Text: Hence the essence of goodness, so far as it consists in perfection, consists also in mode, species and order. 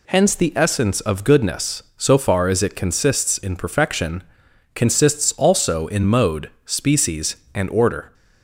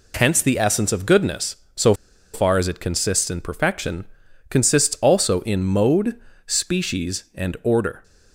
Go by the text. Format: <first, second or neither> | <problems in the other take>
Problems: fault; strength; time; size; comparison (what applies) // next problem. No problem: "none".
first | pauses between "so" and "far"; at 1.9 s; 0.40 s long